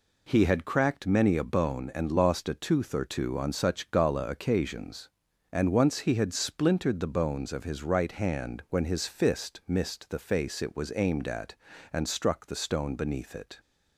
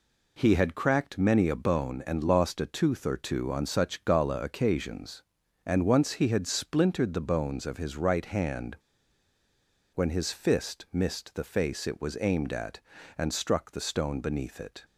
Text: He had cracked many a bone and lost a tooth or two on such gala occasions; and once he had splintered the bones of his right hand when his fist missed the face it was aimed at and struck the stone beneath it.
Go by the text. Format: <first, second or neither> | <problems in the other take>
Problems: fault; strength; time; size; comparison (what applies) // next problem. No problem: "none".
first | pauses between "hand" and "when"; at 8.7 s; 1.1 s long